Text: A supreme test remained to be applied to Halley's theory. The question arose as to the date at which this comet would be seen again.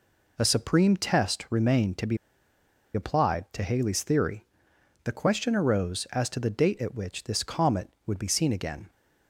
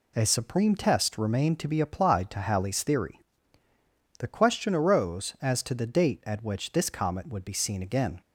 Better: second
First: pauses between "be" and "applied"; noticeable; at 2.1 s; 0.77 s long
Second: none

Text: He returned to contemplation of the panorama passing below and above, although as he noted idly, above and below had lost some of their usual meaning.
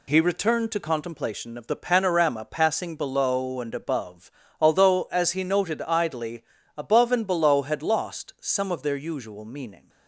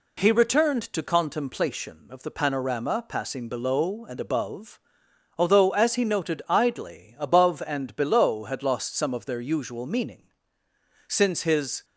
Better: first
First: none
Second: goes on to say "Since his"; noticeable; from 11.0 s on; 0.78 s long

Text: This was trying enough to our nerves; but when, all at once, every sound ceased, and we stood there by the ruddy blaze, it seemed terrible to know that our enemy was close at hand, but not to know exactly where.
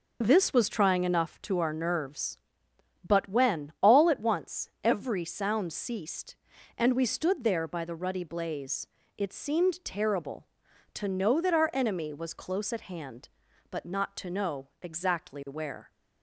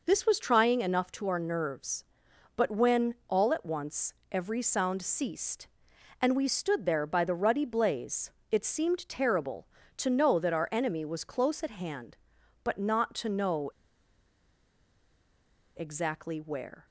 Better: first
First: none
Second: pauses between "know" and "exactly"; strong; at 13.7 s; 2.0 s long

